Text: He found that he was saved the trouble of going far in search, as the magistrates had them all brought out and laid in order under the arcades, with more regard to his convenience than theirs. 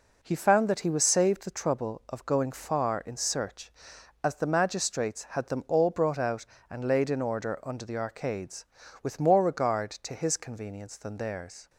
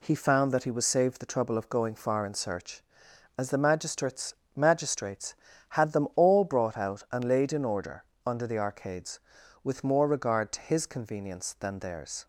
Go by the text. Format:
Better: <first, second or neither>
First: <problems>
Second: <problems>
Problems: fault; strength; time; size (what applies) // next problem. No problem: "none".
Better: first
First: none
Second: says "magistrates" twice; at 4.5 s // pauses between "order" and "under"; slight; at 8.0 s; 0.24 s long